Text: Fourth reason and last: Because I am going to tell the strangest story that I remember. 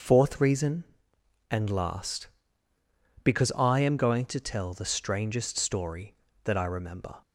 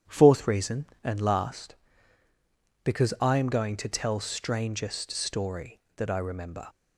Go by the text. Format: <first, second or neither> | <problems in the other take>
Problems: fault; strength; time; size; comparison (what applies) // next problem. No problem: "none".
first | starts louder than the rest; strong; until 1.2 s; 9 dB // skips "the"; at 4.2 s